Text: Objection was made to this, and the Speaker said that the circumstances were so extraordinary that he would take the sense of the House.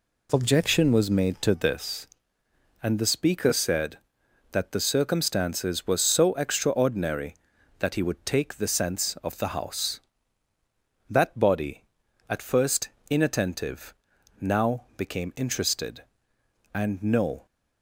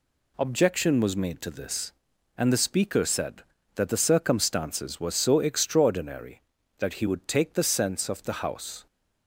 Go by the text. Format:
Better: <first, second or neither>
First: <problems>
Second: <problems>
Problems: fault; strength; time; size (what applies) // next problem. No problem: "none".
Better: second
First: goes on to say "That body at first inattentive now became interested and no"; strong; from 11.0 s on; 6.3 s long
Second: none